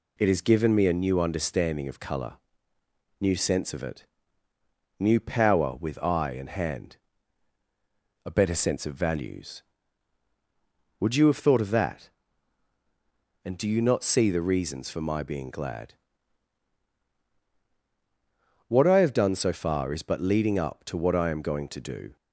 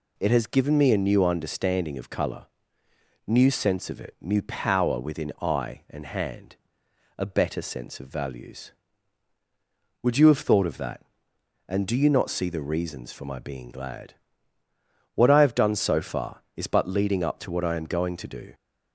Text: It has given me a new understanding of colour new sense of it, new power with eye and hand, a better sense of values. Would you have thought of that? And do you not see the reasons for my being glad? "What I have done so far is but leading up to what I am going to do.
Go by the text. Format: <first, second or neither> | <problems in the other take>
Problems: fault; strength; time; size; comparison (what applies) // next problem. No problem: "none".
first | pauses between "colour" and "new"; noticeable; at 2.4 s; 0.82 s long; noticeable in the first // says "within" for "with"; at 4.9 s